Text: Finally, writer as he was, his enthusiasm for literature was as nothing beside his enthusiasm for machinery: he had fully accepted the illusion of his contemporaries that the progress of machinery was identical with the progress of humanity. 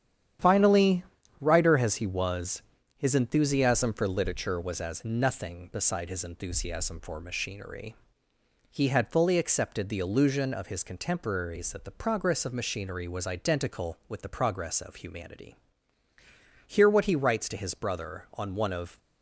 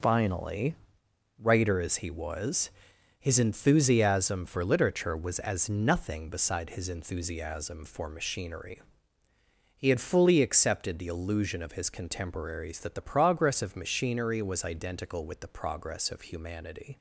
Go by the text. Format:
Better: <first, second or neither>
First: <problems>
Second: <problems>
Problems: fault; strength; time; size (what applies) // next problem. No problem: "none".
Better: second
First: starts louder than the rest; strong; until 1.7 s; 10 dB // goes on to say "Hear what he writes to his brother on one of"; strong; from 16.6 s on; 2.3 s long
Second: none